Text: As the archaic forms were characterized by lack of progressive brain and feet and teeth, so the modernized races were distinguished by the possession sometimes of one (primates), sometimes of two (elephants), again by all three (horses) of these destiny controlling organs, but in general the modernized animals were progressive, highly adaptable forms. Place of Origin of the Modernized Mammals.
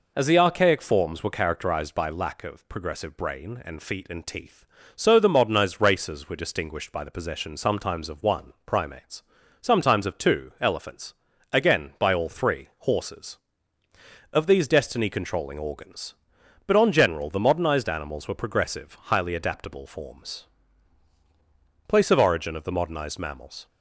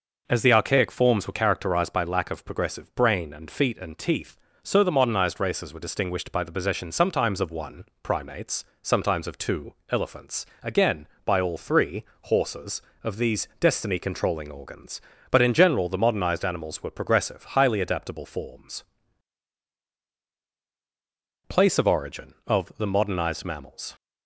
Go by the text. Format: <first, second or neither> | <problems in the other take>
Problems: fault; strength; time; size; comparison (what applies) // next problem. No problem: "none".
second | says "on" for "in"; at 16.7 s